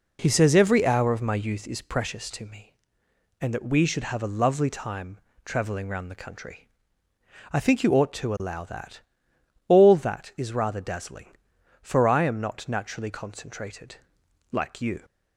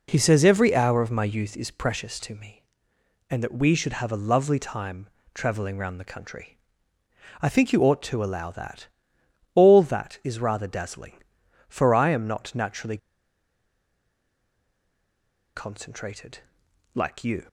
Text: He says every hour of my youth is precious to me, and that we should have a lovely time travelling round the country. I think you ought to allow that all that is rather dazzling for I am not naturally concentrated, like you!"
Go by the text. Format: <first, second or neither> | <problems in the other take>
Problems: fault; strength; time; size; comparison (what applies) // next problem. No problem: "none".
first | pauses between "time" and "travelling"; slight; at 5.0 s; 0.28 s long; slight in the first // pauses between "that" and "all"; noticeable; at 8.8 s; 0.66 s long; noticeable in the first // pauses between "naturally" and "concentrated"; strong; at 12.9 s; 2.5 s long